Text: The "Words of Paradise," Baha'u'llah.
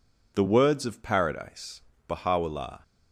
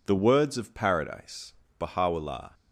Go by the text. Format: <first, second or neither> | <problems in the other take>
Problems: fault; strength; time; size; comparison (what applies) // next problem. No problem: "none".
neither | none